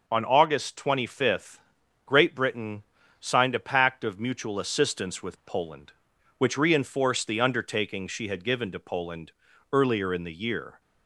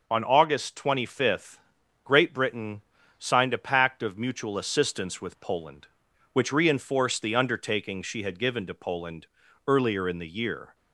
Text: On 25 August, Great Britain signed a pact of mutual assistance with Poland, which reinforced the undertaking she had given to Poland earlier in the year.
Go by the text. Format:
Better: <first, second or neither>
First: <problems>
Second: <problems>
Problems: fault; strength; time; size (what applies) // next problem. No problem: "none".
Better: neither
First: pauses between "Britain" and "signed"; slight; at 2.8 s; 0.34 s long // pauses between "Poland" and "earlier"; at 9.2 s; 0.42 s long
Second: pauses between "Britain" and "signed"; slight; at 2.8 s; 0.34 s long // pauses between "Poland" and "earlier"; at 9.2 s; 0.42 s long